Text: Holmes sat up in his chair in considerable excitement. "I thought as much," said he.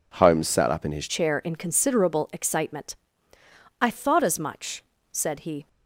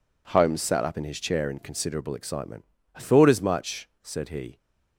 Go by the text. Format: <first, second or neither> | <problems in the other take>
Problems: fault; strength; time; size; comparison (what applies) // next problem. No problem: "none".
second | changes voice at "chair"; from 1.0 s on; 4.6 s long